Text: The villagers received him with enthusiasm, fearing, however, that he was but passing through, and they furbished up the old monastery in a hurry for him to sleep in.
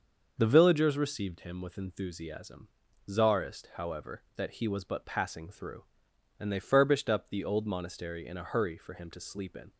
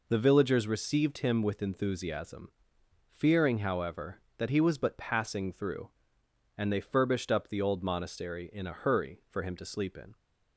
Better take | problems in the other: second | starts louder than the rest; until 1.3 s; 6.5 dB // says "czarist" for "fearing"; at 3.0 s

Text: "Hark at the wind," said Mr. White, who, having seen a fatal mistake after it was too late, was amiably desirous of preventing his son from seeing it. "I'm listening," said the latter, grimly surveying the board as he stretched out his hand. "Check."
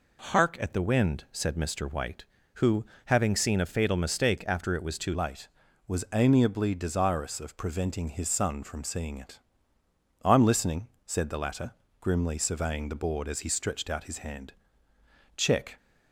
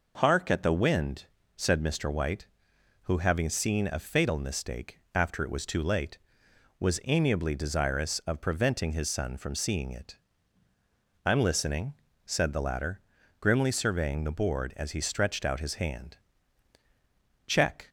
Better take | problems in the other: second | changes voice at "late"; from 5.1 s on; 10.6 s long

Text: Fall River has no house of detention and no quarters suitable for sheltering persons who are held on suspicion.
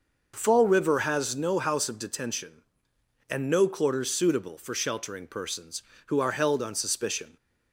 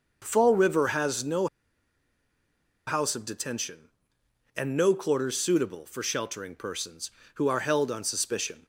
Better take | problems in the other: first | pauses between "no" and "house"; strong; at 1.4 s; 1.4 s long

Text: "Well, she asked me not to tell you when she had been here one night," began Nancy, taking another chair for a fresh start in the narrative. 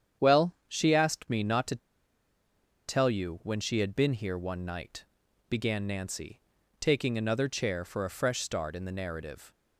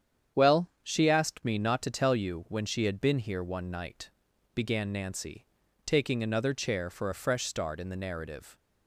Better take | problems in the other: second | starts louder than the rest; strong; until 1.3 s; 8.5 dB; strong in the second // pauses between "to" and "tell"; at 1.7 s; 1.1 s long

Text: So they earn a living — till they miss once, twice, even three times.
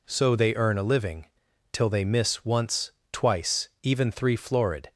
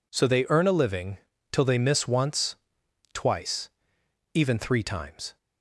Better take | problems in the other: second | says "florid" for "times"; at 4.3 s

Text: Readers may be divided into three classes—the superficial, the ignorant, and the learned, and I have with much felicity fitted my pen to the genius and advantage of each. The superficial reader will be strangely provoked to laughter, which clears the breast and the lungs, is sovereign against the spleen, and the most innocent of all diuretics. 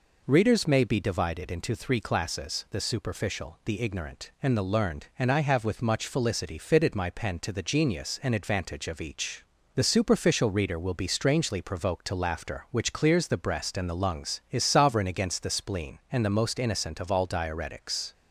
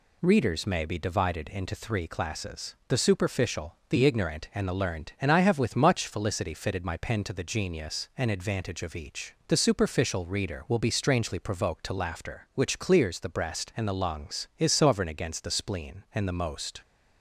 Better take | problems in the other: first | stops before "innocent of all diuretics"; at 16.8 s

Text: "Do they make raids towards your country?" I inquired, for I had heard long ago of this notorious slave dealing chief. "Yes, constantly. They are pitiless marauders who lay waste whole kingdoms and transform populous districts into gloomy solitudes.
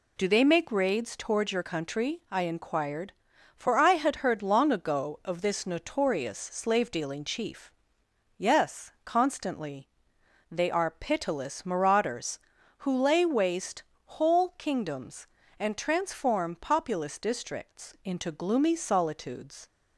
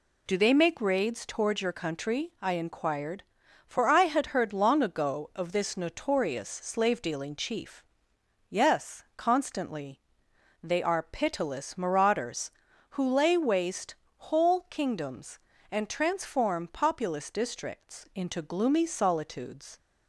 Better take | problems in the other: neither | pauses between "waste" and "whole"; slight; the same in both

